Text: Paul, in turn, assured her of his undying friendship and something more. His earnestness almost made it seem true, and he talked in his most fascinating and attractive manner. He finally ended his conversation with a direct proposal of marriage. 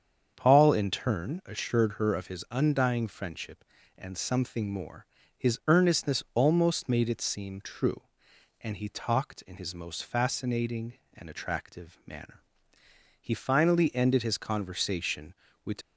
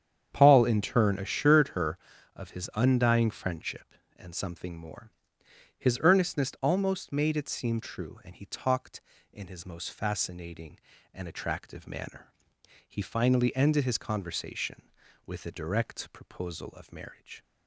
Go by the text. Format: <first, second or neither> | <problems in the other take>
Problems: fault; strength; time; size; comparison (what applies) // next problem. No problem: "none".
second | starts louder than the rest; strong; until 1.3 s; 7.5 dB; strong in the second // stops before "a direct proposal of marriage"; at 15.8 s